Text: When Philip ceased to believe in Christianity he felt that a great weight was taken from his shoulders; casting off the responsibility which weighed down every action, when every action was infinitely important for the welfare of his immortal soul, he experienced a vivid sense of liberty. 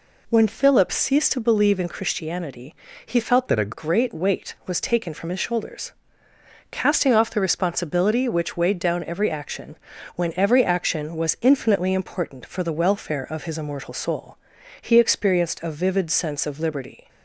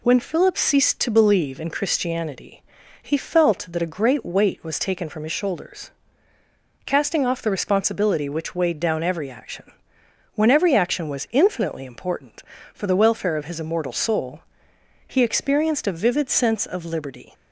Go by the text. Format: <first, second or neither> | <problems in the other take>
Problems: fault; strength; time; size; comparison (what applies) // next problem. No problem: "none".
second | pauses between "Christianity" and "he"; slight; at 2.7 s; 0.32 s long; also in the second // changes voice from "that" to "a"; from 3.4 to 3.7 s; 0.3 s long